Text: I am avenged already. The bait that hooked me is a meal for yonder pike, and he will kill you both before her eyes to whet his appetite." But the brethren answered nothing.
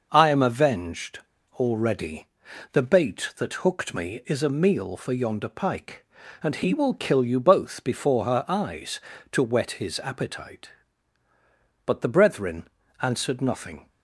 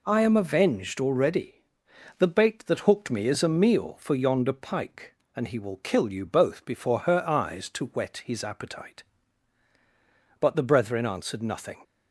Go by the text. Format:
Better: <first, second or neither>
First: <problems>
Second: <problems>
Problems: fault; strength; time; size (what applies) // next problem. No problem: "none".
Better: second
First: pauses between "avenged" and "already"; at 1.1 s; 0.36 s long // pauses between "brethren" and "answered"; slight; at 12.6 s; 0.34 s long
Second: none